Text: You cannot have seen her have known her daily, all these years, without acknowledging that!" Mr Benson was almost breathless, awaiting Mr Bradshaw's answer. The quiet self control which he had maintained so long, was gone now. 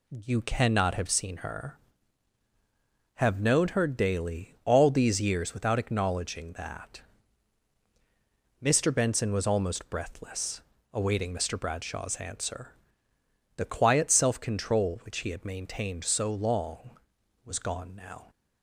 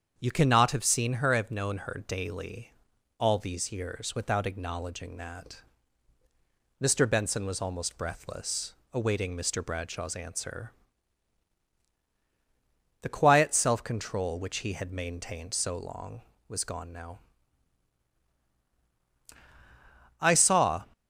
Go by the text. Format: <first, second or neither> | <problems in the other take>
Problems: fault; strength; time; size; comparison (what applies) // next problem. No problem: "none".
first | starts louder than the rest; strong; until 1.1 s; 7.5 dB // goes on to say "I saw"; noticeable; from 20.1 s on; 0.64 s long